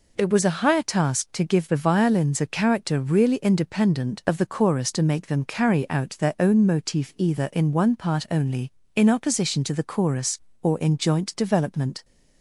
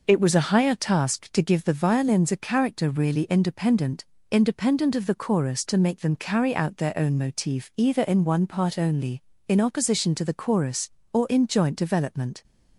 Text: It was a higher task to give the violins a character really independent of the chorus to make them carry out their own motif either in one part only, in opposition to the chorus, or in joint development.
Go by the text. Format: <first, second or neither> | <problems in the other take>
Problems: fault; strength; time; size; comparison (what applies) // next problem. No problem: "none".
first | says "independent" twice; at 4.3 s